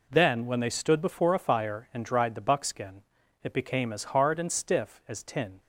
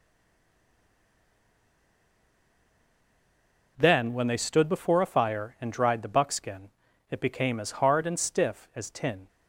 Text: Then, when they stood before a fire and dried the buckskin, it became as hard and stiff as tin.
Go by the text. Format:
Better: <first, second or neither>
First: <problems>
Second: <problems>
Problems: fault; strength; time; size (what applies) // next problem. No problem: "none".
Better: first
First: none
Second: stays silent before the first word; strong; until 3.7 s; 3.7 s long